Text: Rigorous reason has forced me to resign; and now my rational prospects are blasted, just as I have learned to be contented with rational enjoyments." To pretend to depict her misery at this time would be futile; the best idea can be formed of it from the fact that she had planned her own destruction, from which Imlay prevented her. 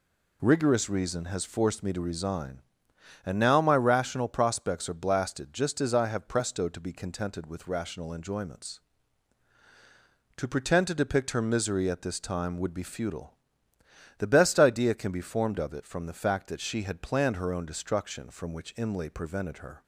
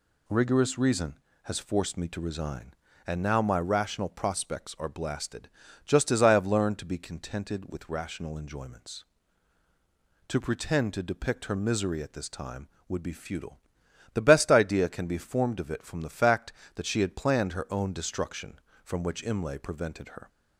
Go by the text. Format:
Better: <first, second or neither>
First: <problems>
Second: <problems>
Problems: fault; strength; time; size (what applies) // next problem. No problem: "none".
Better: second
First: says "presto" for "learned"; at 6.2 s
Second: none